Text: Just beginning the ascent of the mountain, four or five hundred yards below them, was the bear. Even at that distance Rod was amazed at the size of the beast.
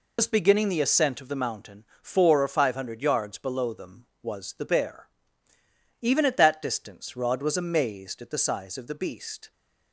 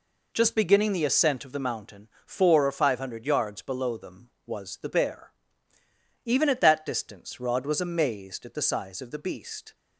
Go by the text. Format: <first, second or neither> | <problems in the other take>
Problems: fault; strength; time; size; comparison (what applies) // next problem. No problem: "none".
second | loses the start of "Just"; at 0.1 s; 95 ms